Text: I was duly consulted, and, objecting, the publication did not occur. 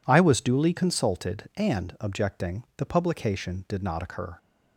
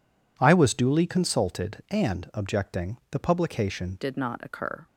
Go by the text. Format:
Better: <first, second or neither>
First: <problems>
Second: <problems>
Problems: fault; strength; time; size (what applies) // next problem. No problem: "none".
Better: first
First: none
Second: changes voice at "did"; from 4.0 s on; 0.8 s long